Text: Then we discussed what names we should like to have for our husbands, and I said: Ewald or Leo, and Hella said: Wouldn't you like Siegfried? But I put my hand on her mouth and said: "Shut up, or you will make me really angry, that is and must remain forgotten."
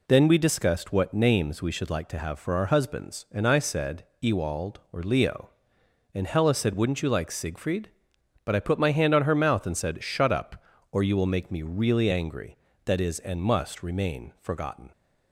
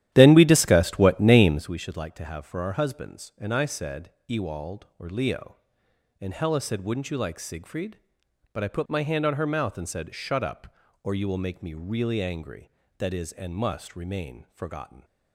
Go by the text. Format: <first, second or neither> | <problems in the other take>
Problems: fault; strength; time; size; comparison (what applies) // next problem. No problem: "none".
first | starts louder than the rest; strong; until 1.7 s; 12.5 dB